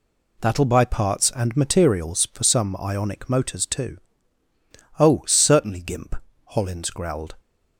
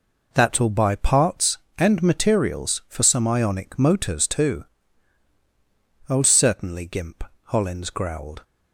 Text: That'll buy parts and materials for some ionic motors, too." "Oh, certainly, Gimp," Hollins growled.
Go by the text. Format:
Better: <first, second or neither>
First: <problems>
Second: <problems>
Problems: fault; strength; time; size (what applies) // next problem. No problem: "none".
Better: neither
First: none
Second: none